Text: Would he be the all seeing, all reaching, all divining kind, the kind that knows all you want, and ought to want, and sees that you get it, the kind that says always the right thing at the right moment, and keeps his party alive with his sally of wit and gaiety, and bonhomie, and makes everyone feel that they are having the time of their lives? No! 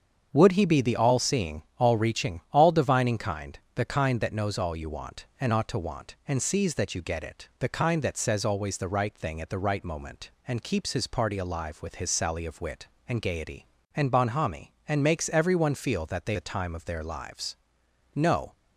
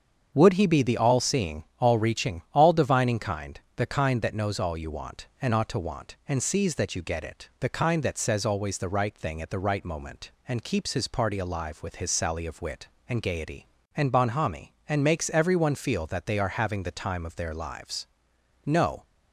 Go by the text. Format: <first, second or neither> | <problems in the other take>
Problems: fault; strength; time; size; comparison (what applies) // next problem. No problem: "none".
second | starts louder than the rest; strong; until 1.3 s; 7 dB; strong in the second // skips "are having"; at 16.3 s